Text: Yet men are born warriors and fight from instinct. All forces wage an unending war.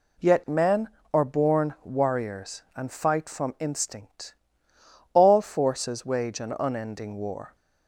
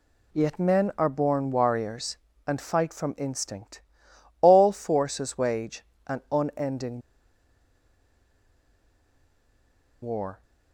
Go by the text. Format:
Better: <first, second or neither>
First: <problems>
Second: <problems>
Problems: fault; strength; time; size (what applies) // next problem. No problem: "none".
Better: first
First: none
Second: pauses between "wage" and "an"; slight; at 5.8 s; 0.24 s long // pauses between "unending" and "war"; strong; at 7.0 s; 3.0 s long